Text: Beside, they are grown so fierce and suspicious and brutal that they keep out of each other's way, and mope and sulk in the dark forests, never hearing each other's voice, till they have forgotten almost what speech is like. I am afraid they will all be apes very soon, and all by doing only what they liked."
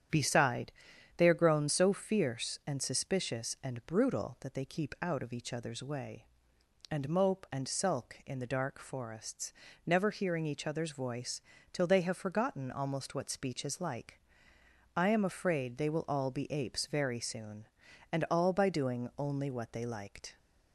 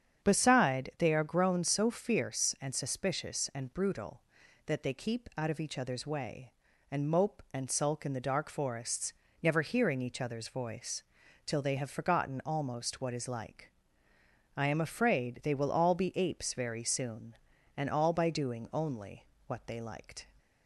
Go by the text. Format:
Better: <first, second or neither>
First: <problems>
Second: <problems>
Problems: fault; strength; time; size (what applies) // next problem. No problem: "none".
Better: first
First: starts louder than the rest; strong; until 1.5 s; 9 dB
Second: starts louder than the rest; strong; until 1.3 s; 8 dB // skips "speech"; at 13.1 s // pauses between "only" and "what"; slight; at 19.2 s; 0.22 s long